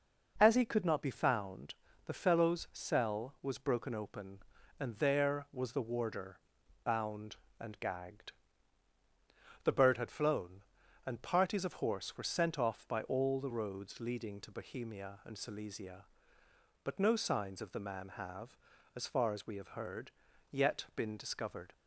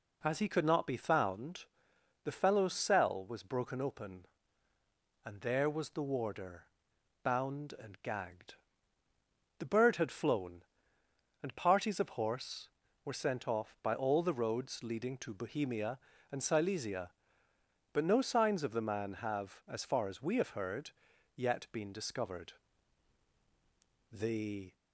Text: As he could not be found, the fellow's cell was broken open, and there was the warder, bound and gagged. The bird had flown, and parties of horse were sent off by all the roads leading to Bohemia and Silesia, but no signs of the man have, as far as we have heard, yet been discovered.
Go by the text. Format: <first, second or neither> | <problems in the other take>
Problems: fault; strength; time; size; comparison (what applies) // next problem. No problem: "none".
first | goes on to say "The"; noticeable; from 24.1 s on; 0.64 s long